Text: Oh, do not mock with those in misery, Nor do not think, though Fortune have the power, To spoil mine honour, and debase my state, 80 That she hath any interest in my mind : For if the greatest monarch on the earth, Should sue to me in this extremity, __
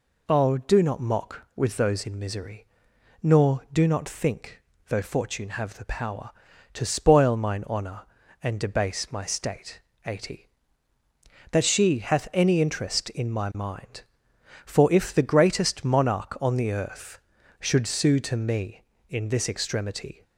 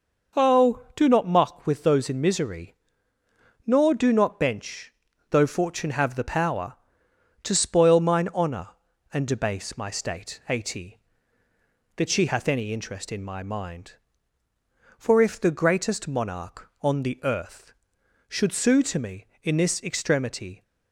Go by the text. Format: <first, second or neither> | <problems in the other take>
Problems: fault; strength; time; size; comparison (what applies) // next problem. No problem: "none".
first | says "bench" for "think"; at 4.3 s